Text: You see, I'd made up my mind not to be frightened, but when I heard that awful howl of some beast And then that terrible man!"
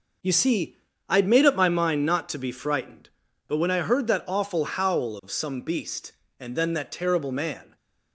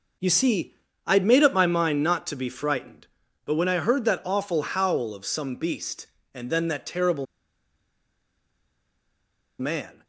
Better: first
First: none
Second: pauses between "terrible" and "man"; strong; at 7.2 s; 2.3 s long

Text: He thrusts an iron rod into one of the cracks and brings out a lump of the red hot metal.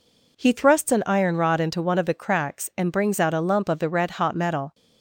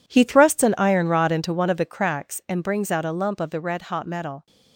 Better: first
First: none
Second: gets quieter; strong; throughout; 13 dB

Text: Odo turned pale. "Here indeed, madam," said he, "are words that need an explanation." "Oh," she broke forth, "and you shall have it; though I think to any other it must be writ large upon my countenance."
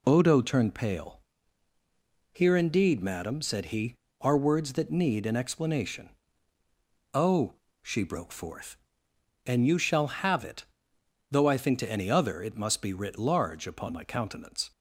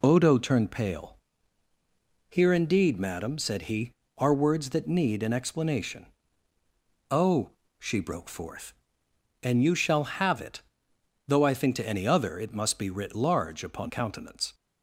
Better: first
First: none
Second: skips "my"; at 13.8 s

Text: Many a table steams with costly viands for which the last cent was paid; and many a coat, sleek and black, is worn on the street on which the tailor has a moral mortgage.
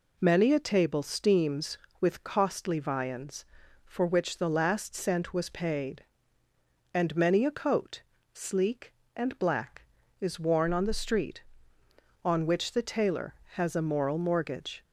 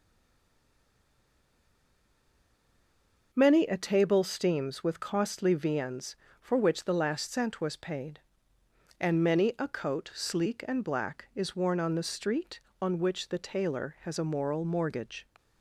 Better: first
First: none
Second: stays silent before the first word; strong; until 3.3 s; 3.3 s long

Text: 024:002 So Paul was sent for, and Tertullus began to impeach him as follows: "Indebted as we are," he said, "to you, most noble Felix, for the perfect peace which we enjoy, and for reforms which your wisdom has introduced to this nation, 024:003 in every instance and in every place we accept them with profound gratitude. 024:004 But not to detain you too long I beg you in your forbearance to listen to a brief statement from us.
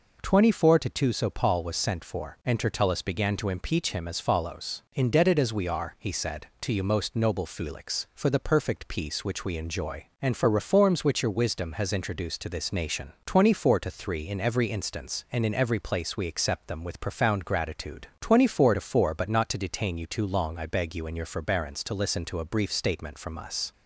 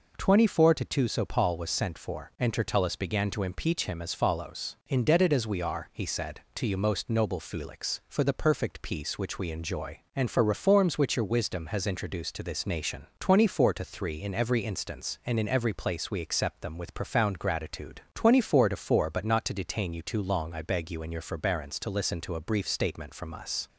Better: neither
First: none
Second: none

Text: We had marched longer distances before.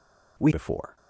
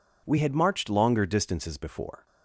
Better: second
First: skips "had marched longer distances"; at 0.5 s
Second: none

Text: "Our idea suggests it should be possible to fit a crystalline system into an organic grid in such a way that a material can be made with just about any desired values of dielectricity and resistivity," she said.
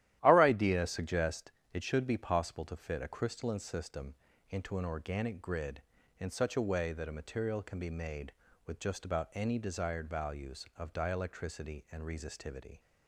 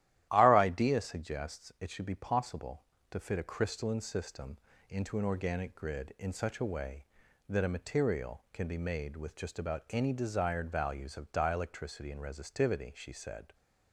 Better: second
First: starts louder than the rest; strong; until 1.2 s; 13 dB // pauses between "suggests" and "it"; slight; at 1.4 s; 0.24 s long // pauses between "system" and "into"; slight; at 4.1 s; 0.34 s long // stops before "she said"; at 12.7 s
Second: starts louder than the rest; strong; until 1.3 s; 13.5 dB // pauses between "system" and "into"; slight; at 4.5 s; 0.32 s long

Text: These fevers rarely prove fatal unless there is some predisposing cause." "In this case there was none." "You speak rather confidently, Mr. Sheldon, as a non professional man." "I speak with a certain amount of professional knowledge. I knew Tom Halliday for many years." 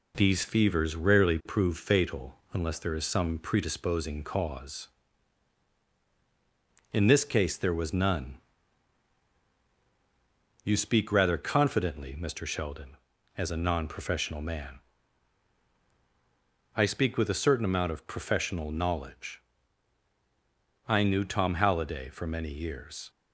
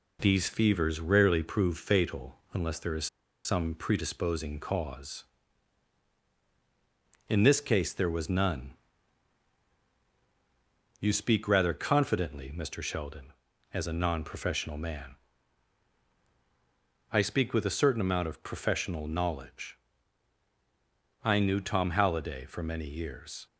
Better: first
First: pauses between "fatal" and "unless"; slight; at 2.3 s; 0.16 s long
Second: pauses between "fatal" and "unless"; slight; at 2.3 s; 0.16 s long // pauses between "is" and "some"; at 3.0 s; 0.38 s long

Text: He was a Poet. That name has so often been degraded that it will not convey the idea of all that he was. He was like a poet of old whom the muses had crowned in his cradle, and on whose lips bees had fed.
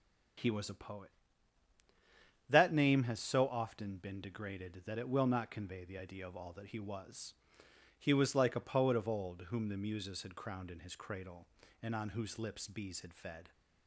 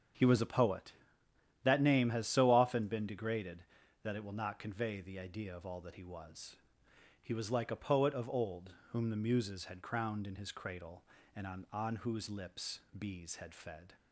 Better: first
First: starts louder than the rest; strong; until 2.7 s; 7 dB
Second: starts louder than the rest; strong; until 1.8 s; 7 dB // pauses between "old" and "whom"; slight; at 8.7 s; 0.18 s long // says "on" twice; at 11.7 s // pauses between "lips" and "bees"; slight; at 12.7 s; 0.18 s long

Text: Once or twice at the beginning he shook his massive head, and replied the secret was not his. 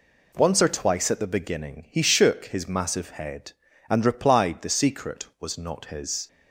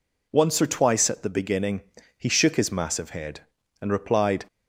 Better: first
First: none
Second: pauses between "beginning" and "he"; at 1.7 s; 0.38 s long // stops before "the secret was not his"; at 4.4 s

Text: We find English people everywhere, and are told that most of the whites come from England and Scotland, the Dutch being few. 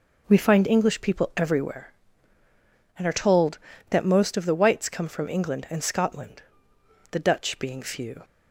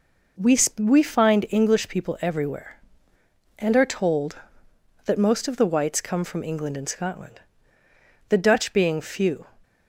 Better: first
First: none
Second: says "We" twice; at 0.7 s

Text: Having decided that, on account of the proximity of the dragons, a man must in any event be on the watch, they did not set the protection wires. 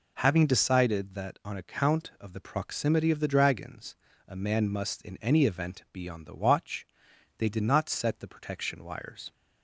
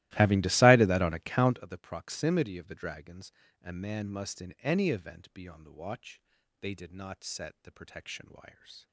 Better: first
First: none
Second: starts louder than the rest; strong; until 1.6 s; 16.5 dB

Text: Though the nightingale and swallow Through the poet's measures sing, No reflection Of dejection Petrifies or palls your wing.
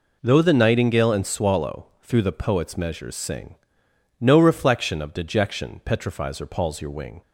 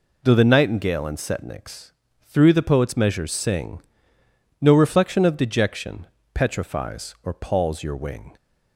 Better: first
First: none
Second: says "setniks" for "swallow"; at 1.1 s // pauses between "dejection" and "Petrifies"; slight; at 6.0 s; 0.26 s long

